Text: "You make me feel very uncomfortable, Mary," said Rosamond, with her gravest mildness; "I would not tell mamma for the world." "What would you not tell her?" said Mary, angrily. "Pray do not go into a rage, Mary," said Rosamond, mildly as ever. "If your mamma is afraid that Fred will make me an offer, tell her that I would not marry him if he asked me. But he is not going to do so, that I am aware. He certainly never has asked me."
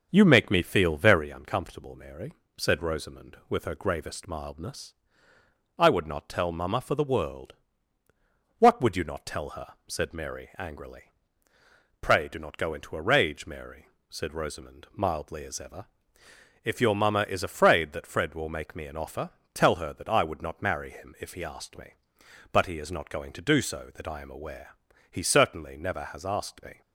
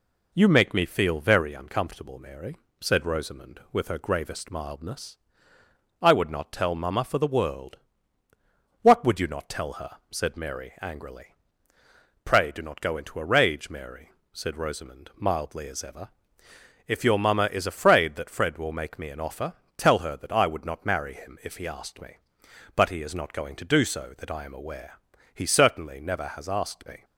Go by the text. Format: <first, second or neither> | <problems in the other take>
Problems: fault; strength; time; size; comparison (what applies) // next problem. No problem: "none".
second | starts louder than the rest; until 1.3 s; 6.5 dB